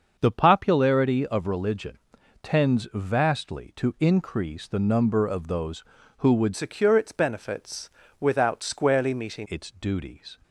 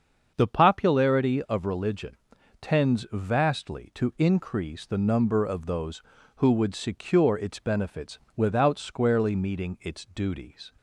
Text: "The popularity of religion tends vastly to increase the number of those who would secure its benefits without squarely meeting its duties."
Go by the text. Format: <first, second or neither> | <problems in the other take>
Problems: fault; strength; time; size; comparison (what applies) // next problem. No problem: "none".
second | starts louder than the rest; until 1.2 s; 6.5 dB; also in the second // pauses between "religion" and "tends"; at 1.9 s; 0.42 s long; also in the second // changes voice from "secure" to "meeting"; from 6.5 to 9.4 s; 2.9 s long // pauses between "benefits" and "without"; slight; at 7.8 s; 0.32 s long; slight in the second